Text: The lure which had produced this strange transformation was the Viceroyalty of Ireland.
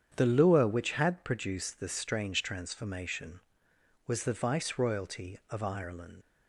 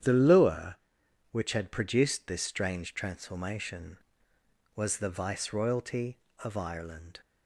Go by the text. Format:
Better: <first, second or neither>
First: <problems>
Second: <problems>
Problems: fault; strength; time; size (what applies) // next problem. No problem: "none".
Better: second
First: starts louder than the rest; strong; until 1.1 s; 8.5 dB // leaves "Ireland" unfinished; at 6.2 s; 80 ms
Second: starts louder than the rest; strong; until 1.5 s; 9.5 dB